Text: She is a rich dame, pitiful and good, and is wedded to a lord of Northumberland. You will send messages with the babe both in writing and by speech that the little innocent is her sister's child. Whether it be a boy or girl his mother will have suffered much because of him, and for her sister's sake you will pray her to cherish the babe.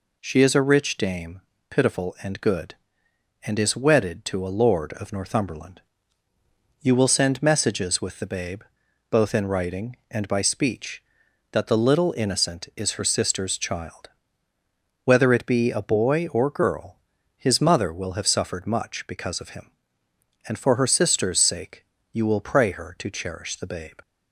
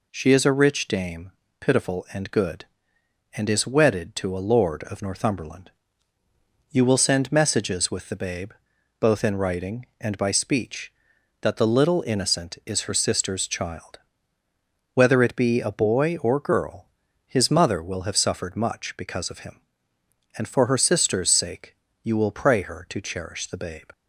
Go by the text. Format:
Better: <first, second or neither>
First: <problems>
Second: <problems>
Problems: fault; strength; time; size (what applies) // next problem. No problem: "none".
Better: neither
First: pauses between "babe" and "both"; noticeable; at 8.6 s; 0.48 s long // pauses between "girl" and "his"; at 16.9 s; 0.38 s long // pauses between "sake" and "you"; slight; at 21.8 s; 0.28 s long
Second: pauses between "babe" and "both"; noticeable; at 8.5 s; 0.48 s long // pauses between "girl" and "his"; at 16.8 s; 0.38 s long // pauses between "sake" and "you"; slight; at 21.7 s; 0.28 s long